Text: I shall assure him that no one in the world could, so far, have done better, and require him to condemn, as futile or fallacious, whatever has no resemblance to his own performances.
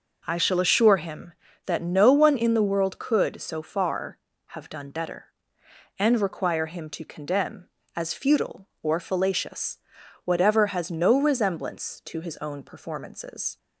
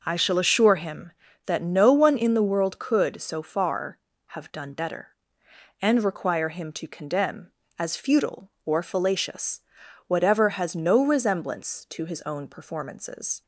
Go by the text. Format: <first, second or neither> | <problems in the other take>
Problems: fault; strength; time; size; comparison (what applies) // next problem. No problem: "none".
neither | none